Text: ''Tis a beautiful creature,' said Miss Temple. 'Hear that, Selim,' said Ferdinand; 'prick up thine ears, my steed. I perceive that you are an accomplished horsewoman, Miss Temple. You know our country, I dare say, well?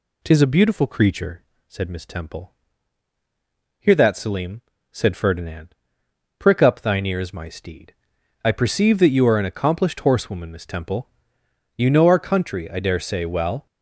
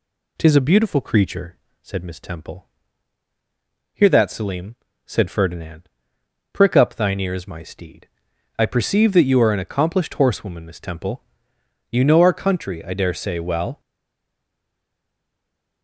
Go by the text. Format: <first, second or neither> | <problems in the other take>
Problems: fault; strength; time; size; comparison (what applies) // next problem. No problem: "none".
first | stays silent after the last word; noticeable; from 13.7 s on; 2.1 s long